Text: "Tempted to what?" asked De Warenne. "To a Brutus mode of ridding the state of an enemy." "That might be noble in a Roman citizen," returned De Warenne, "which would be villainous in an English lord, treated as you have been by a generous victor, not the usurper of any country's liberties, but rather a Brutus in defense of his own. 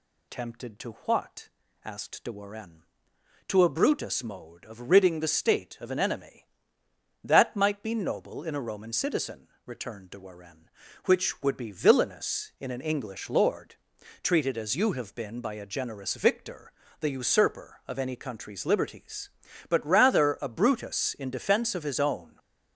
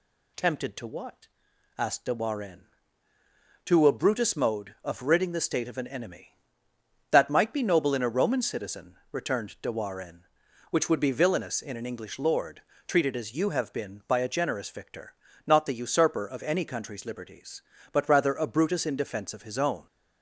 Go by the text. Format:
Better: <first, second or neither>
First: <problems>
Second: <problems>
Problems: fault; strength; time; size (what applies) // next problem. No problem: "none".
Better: second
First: skips "not"; at 16.8 s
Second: none